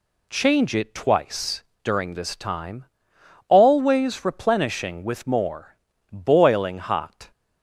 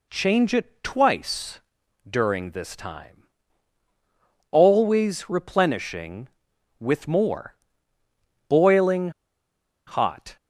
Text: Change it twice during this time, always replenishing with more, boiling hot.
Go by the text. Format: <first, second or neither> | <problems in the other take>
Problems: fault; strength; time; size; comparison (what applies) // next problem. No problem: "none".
first | pauses between "twice" and "during"; noticeable; at 1.5 s; 0.48 s long; slight in the first // pauses between "boiling" and "hot"; noticeable; at 9.0 s; 0.77 s long